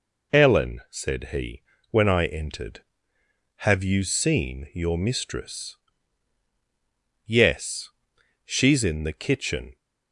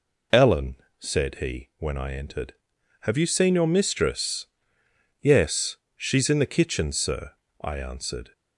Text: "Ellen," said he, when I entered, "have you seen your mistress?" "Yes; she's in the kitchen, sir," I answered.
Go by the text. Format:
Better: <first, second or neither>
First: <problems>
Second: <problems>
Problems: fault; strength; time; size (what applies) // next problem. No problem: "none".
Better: second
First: stops before "sir I answered"; at 9.7 s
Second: none